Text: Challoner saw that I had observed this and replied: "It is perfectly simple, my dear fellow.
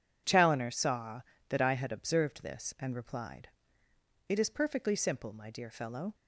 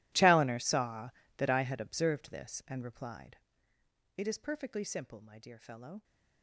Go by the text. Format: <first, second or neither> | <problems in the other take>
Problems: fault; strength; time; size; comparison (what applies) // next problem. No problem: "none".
first | gets quieter; strong; throughout; 22 dB